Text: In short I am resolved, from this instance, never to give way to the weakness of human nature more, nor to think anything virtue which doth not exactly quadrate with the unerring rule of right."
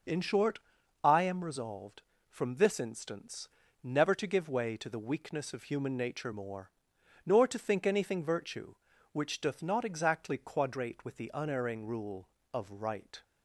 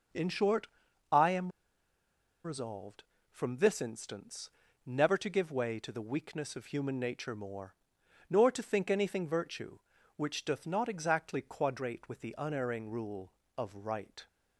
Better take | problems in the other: first | starts louder than the rest; until 2.5 s; 6 dB; noticeable in the first // pauses between "short" and "I"; at 0.6 s; 0.44 s long; also in the first // pauses between "am" and "resolved"; noticeable; at 1.5 s; 0.93 s long

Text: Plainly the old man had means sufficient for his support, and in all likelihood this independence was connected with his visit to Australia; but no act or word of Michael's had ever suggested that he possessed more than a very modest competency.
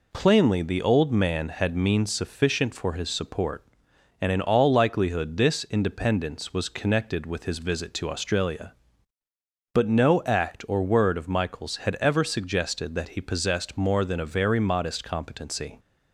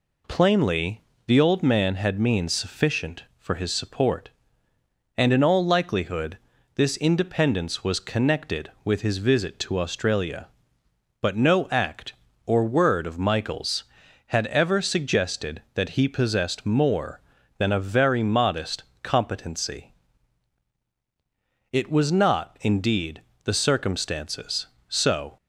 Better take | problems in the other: first | pauses between "Plainly" and "the"; slight; at 1.0 s; 0.26 s long // pauses between "likelihood" and "this"; slight; at 6.3 s; 0.36 s long // pauses between "modest" and "competency"; slight; at 18.8 s; 0.20 s long // goes on to say "It was not indeed the circumstances so"; strong; from 21.7 s on; 3.6 s long

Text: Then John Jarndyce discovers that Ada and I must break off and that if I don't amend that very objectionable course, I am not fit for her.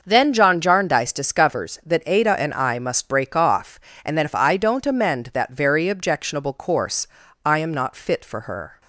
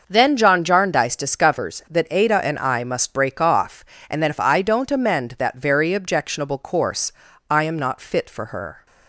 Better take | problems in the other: neither | starts louder than the rest; noticeable; the same in both

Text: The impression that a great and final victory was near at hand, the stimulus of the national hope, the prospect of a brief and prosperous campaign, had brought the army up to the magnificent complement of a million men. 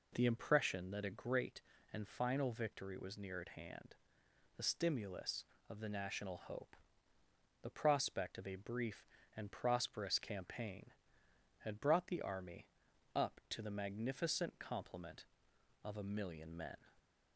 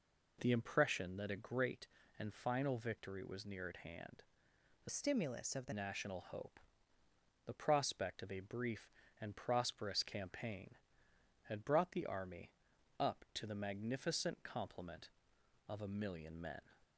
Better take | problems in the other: first | changes voice from "stimulus" to "the"; from 4.8 to 5.7 s; 0.9 s long // pauses between "army" and "up"; noticeable; at 12.5 s; 0.48 s long; noticeable in the first

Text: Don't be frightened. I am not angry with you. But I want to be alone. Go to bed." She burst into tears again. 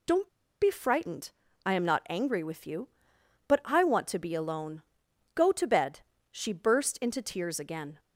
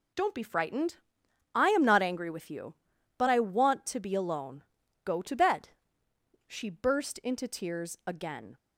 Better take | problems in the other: second | pauses between "Don't" and "be"; slight; at 0.2 s; 0.33 s long

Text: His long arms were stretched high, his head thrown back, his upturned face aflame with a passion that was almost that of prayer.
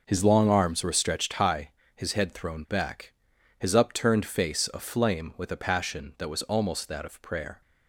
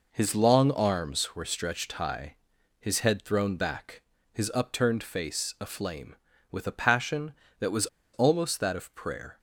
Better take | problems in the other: first | pauses between "was" and "almost"; slight; at 7.8 s; 0.27 s long

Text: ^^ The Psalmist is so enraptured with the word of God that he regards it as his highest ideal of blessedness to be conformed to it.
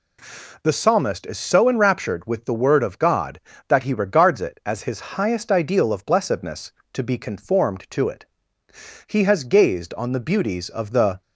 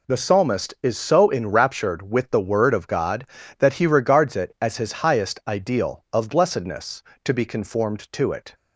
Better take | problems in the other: second | goes on to say "He has gazed on the beauties of the"; strong; from 9.0 s on; 2.1 s long

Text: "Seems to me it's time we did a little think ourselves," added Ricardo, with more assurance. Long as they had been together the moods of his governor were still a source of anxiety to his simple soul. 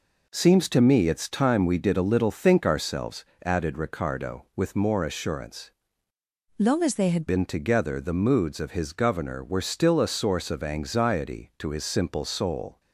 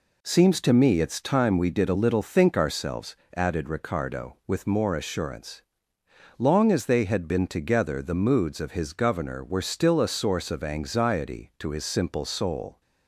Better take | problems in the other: second | changes voice from "Long" to "had"; from 6.5 to 7.2 s; 0.7 s long

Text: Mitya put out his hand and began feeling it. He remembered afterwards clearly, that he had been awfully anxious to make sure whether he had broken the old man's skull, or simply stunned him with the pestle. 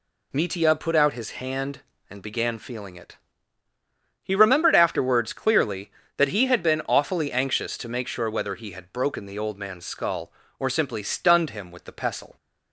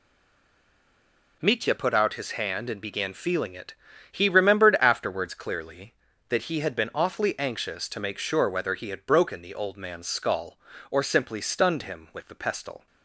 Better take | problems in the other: first | stays silent before the first word; noticeable; until 1.4 s; 1.4 s long

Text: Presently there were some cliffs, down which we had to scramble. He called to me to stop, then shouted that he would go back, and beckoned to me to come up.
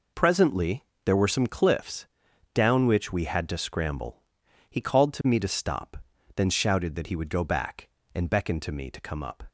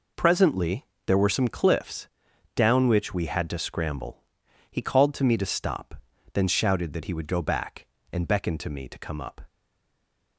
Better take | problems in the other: first | pauses between "Presently" and "there"; slight; at 0.8 s; 0.22 s long; slight in the first // stays silent after the last word; slight; from 9.4 s on; 0.9 s long

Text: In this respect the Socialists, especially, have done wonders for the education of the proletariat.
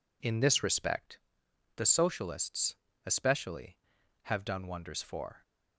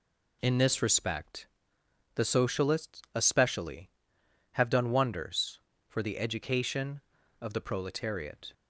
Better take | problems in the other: second | pauses between "respect" and "the"; noticeable; at 1.1 s; 0.58 s long; noticeable in the second // stops before "the education of the proletariat"; at 5.4 s

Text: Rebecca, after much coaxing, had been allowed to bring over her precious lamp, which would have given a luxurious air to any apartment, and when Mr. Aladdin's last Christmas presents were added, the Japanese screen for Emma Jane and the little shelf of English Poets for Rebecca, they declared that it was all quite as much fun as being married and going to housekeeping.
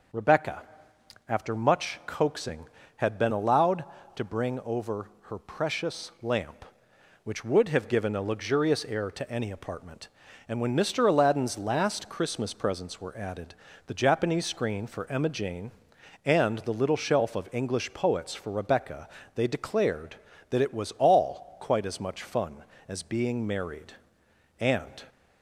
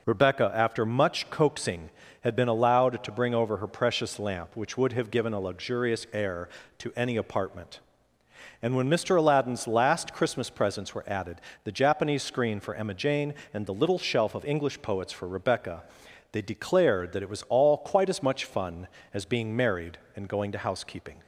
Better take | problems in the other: second | starts louder than the rest; until 1.8 s; 6.5 dB // pauses between "over" and "her"; slight; at 5.0 s; 0.22 s long // stops before "going to housekeeping"; at 25.0 s

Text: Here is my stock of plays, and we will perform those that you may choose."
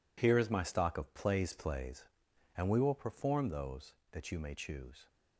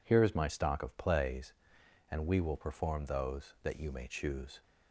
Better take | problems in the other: second | says "plays" twice; at 1.5 s

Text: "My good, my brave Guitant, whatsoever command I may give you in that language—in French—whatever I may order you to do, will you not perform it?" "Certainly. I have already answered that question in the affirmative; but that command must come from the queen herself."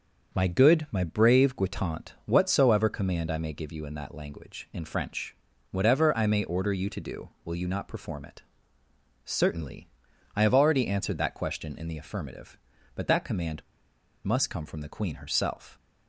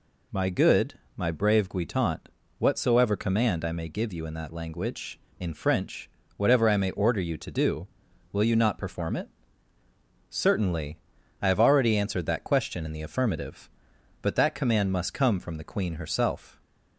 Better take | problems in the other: second | starts louder than the rest; until 1.4 s; 7 dB // pauses between "command" and "must"; noticeable; at 13.6 s; 0.62 s long

